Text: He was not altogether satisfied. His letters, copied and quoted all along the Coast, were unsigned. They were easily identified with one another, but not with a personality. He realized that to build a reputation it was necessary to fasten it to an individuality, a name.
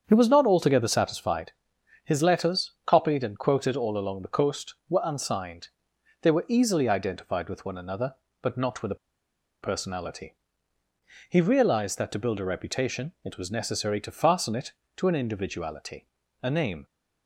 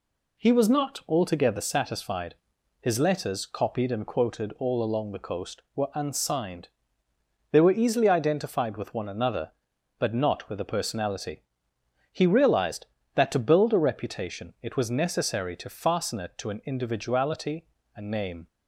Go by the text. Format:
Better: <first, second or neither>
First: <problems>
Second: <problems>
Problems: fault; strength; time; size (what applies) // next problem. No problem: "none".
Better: second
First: starts louder than the rest; strong; until 1.0 s; 7.5 dB // pauses between "a" and "personality"; noticeable; at 8.9 s; 0.67 s long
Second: none